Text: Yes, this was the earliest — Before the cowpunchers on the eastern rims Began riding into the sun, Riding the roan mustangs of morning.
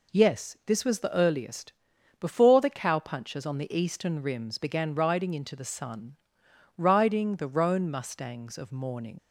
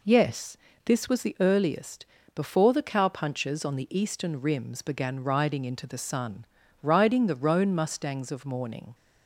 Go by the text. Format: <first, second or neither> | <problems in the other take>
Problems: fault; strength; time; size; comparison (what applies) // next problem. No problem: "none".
second | leaves "morning" unfinished; at 9.1 s; 85 ms